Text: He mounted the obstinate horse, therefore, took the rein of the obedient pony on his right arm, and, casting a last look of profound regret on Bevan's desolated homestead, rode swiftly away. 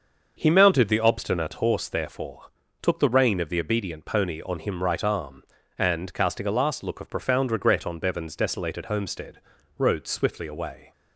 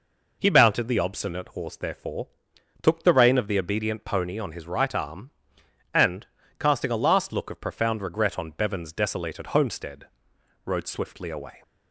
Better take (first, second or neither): second